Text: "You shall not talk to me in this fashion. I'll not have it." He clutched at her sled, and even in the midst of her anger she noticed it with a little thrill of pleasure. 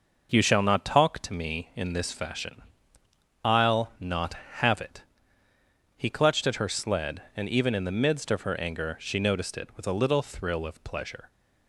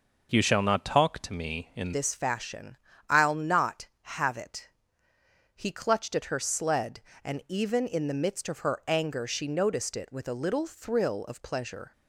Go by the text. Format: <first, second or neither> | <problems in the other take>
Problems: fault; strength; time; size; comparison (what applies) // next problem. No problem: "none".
first | changes voice at "this"; from 1.9 s on; 10.0 s long